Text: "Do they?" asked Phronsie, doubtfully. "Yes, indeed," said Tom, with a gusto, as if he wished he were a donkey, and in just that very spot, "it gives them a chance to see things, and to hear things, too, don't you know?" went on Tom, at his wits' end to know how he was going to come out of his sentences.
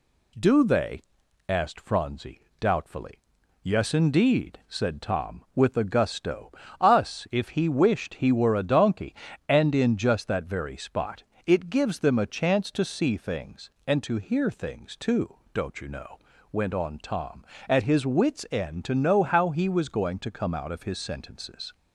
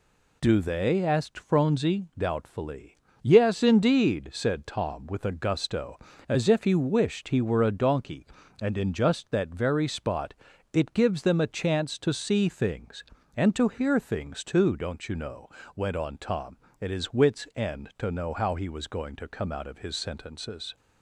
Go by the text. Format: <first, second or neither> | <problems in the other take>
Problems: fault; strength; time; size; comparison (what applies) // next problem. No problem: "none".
second | says "us" for "as"; at 6.8 s